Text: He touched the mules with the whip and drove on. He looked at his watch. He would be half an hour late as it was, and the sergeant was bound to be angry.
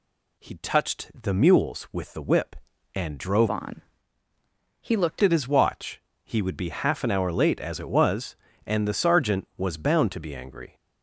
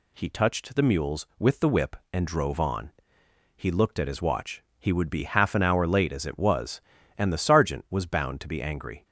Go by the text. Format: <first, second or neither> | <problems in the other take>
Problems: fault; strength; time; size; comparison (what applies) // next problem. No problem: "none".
second | changes voice from "on" to "looked"; from 3.4 to 5.2 s; 1.8 s long